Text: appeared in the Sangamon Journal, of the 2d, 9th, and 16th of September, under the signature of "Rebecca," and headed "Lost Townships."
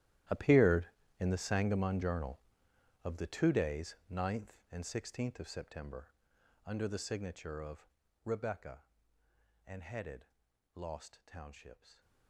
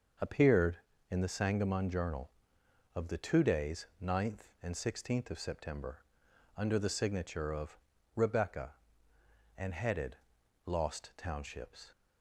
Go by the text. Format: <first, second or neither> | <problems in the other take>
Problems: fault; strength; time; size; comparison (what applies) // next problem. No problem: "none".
second | gets quieter; strong; throughout; 17.5 dB // starts louder than the rest; strong; until 1.6 s; 13 dB; also in the second // pauses between "of" and "Rebecca"; at 7.8 s; 0.38 s long; also in the second // pauses between "headed" and "Lost"; noticeable; at 10.2 s; 0.48 s long; noticeable in the second